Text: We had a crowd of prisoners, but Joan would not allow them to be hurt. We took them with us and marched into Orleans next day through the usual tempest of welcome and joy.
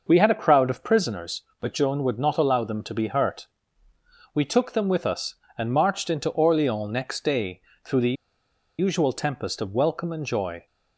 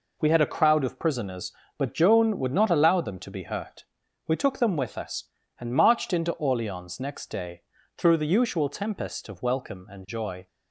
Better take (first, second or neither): second